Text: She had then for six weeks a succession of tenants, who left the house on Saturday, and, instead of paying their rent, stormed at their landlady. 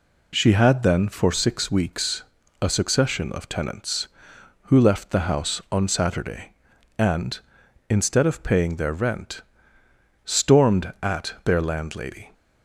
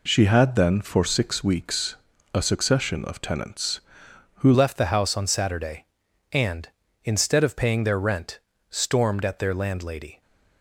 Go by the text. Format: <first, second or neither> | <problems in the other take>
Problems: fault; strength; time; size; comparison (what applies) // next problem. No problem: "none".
first | pauses between "weeks" and "a"; slight; at 1.9 s; 0.36 s long; slight in the first // changes voice at "left"; from 4.5 s on; 5.7 s long